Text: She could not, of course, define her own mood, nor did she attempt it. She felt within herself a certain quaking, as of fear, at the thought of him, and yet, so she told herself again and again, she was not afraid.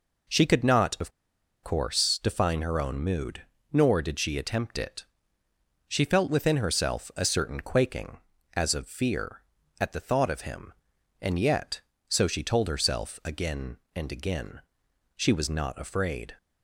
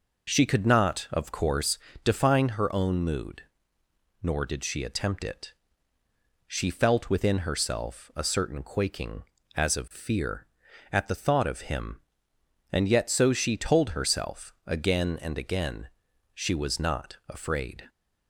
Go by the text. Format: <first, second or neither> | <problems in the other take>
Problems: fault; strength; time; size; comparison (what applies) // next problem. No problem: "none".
second | pauses between "of" and "course"; noticeable; at 1.1 s; 0.52 s long